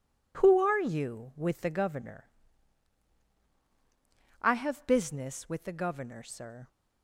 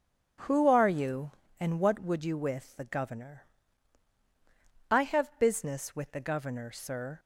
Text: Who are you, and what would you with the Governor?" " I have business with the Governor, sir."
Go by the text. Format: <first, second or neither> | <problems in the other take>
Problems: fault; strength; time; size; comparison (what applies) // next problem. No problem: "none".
second | skips "and what would you"; at 1.3 s